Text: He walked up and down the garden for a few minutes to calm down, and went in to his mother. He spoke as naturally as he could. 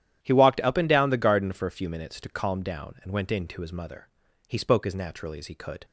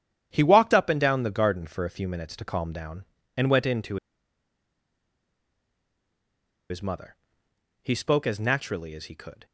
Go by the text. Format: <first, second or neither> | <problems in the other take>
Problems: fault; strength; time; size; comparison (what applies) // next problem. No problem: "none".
first | starts louder than the rest; strong; until 1.3 s; 10 dB; strong in the first // pauses between "to" and "his"; strong; at 3.9 s; 2.7 s long